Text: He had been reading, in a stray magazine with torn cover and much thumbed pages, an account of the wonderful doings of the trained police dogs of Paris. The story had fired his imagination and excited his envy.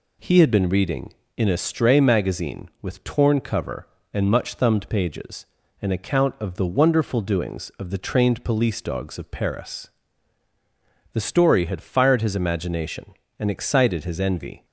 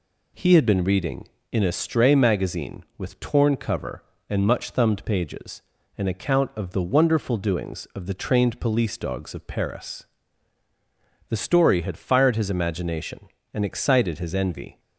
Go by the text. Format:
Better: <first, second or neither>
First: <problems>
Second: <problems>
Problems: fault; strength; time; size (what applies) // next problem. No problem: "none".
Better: neither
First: none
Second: none